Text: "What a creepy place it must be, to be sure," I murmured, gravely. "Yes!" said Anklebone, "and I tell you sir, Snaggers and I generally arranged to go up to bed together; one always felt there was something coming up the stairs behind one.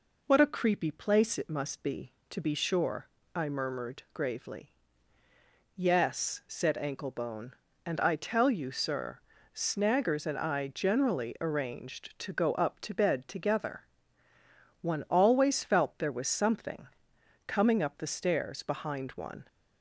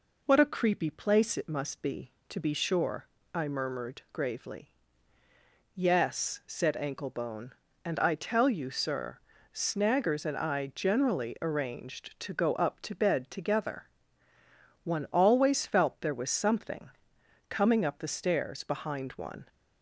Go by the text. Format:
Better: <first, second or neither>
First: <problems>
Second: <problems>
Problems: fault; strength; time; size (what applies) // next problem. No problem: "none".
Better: neither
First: pauses between "something" and "coming"; noticeable; at 16.8 s; 0.58 s long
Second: pauses between "something" and "coming"; noticeable; at 16.9 s; 0.58 s long